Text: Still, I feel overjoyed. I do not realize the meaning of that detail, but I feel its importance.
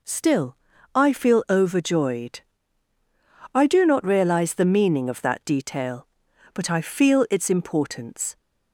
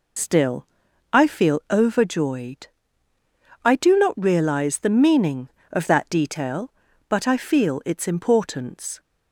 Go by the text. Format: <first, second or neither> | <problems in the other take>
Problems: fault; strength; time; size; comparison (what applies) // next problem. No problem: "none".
first | loses the start of "Still"; at 0.1 s; 70 ms